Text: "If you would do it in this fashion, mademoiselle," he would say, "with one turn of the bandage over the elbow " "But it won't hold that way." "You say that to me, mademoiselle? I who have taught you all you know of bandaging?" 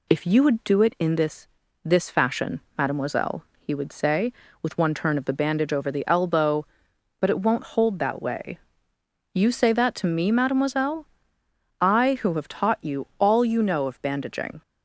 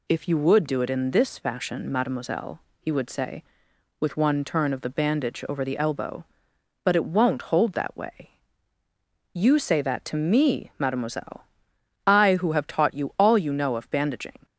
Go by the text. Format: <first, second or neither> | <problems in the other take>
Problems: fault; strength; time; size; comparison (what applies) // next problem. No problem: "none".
second | says "this" twice; at 1.8 s